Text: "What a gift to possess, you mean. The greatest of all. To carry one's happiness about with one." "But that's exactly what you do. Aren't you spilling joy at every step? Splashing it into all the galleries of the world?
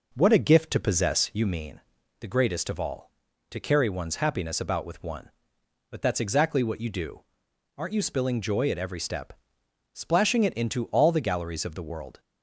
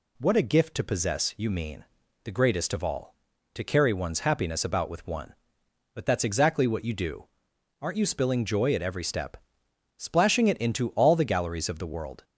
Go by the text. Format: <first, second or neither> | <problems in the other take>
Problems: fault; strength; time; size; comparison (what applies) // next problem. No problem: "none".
second | starts louder than the rest; noticeable; until 1.6 s; 5 dB